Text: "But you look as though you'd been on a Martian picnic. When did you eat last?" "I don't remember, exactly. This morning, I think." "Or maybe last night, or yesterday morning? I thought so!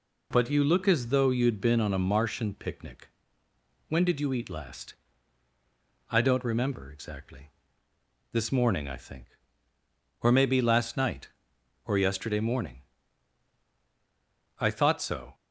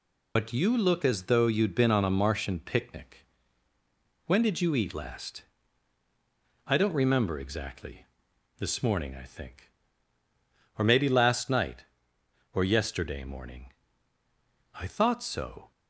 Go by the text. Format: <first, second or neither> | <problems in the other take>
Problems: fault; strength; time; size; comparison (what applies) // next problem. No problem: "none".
first | loses the start of "But"; at 0.3 s; 70 ms